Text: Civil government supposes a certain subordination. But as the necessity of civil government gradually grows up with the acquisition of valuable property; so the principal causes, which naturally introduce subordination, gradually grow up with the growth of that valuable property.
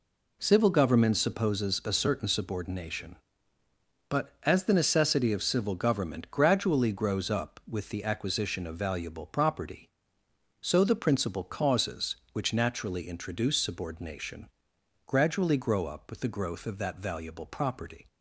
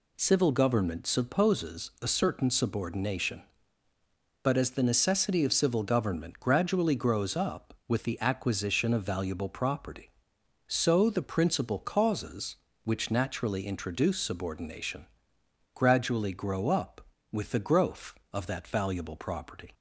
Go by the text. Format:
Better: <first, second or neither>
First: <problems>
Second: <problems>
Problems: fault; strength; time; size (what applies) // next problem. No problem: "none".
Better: neither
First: none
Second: none